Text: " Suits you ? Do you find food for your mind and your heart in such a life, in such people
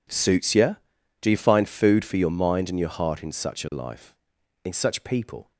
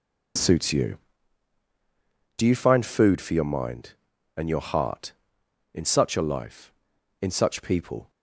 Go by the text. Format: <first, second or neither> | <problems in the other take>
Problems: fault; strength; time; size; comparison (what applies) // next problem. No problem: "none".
neither | none